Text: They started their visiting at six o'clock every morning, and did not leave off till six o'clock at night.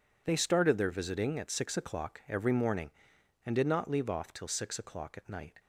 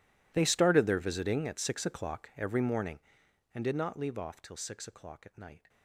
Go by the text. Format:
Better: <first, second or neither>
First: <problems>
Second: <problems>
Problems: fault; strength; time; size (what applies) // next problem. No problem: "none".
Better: first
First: none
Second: gets quieter; strong; throughout; 23.5 dB